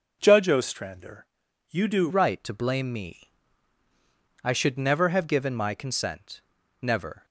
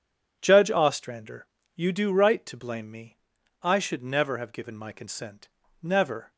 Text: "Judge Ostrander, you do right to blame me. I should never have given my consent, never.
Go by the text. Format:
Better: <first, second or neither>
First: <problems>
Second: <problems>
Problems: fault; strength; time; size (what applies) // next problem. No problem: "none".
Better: second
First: changes voice at "right"; from 2.0 s on; 5.2 s long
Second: none